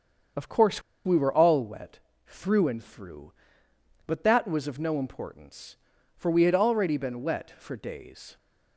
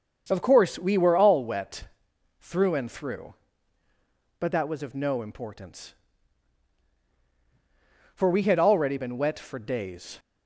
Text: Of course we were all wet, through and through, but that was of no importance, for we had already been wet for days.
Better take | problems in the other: second | starts louder than the rest; strong; until 1.6 s; 7 dB; also in the second // pauses between "course" and "we"; slight; at 0.8 s; 0.24 s long

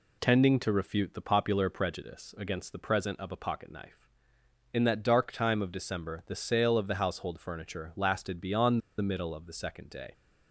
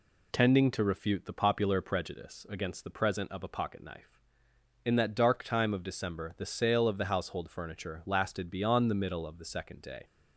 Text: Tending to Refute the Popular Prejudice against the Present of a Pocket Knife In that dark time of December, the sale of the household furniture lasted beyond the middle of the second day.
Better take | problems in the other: second | pauses between "beyond" and "the"; slight; at 8.8 s; 0.18 s long

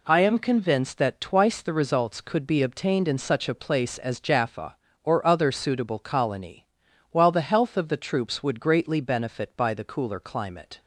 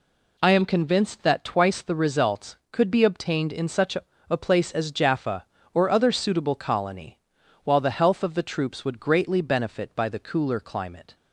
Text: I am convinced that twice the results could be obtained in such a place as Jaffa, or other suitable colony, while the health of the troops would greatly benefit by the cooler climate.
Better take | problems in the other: first | says "a" twice; at 4.2 s

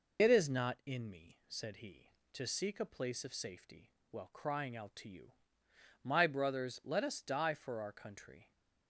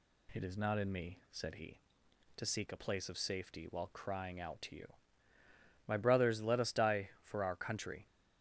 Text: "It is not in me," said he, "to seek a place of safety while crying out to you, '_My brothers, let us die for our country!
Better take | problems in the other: second | loses the start of "It"; at 0.1 s; 65 ms // pauses between "safety" and "while"; slight; at 3.9 s; 0.18 s long

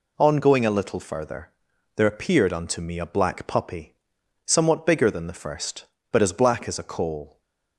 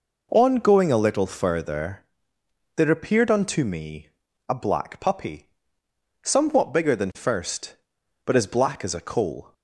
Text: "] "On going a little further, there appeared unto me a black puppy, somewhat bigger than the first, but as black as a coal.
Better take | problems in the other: first | pauses between "me" and "a"; at 4.0 s; 0.38 s long // skips "the"; at 7.1 s

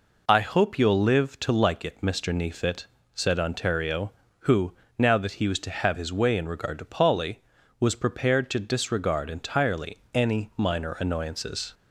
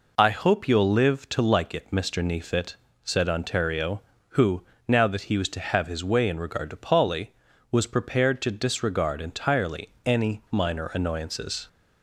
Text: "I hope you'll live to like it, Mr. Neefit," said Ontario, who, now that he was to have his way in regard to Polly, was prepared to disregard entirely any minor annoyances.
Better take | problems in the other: neither | pauses between "entirely" and "any"; slight; the same in both

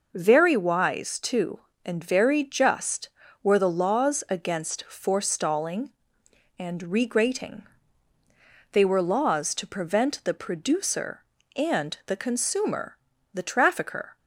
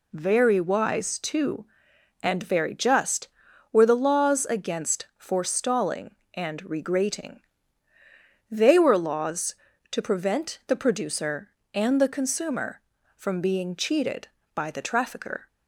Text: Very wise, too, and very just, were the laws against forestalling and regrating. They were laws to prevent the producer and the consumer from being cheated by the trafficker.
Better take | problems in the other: second | skips "from being cheated by"; at 13.1 s

